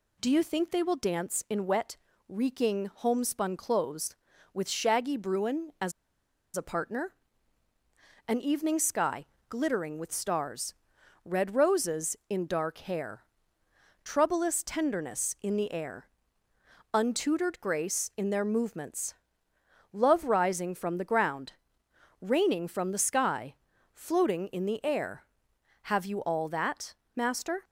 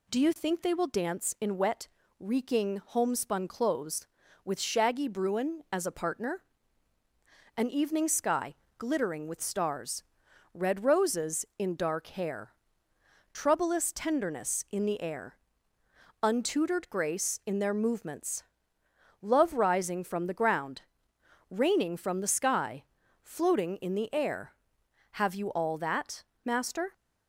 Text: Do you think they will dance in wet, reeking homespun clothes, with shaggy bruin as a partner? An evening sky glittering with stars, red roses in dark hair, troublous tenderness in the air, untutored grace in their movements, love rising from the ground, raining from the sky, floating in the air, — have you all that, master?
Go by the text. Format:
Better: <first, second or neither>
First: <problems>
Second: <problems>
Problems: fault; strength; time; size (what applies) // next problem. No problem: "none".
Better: second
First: pauses between "as" and "a"; noticeable; at 5.9 s; 0.63 s long // pauses between "sky" and "glittering"; slight; at 9.2 s; 0.24 s long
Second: pauses between "sky" and "glittering"; slight; at 8.5 s; 0.24 s long